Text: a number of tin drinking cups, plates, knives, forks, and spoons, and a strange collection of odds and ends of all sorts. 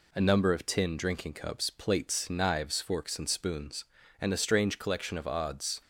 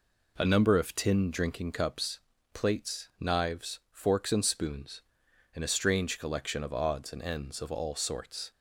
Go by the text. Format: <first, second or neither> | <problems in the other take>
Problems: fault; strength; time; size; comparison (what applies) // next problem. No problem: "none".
second | stops before "and ends of all sorts"; at 5.8 s